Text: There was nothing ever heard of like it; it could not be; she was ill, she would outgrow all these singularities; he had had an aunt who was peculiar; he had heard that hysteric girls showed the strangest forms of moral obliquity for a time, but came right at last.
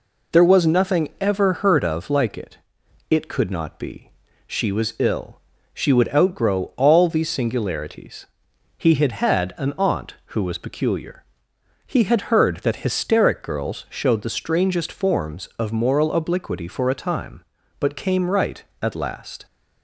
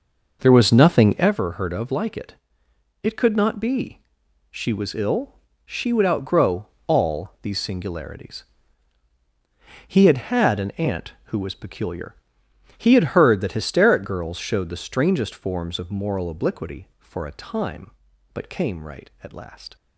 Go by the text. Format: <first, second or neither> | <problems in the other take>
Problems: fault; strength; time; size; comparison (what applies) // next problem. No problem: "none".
first | starts louder than the rest; noticeable; until 1.3 s; 5.5 dB // pauses between "outgrow" and "all"; slight; at 6.6 s; 0.22 s long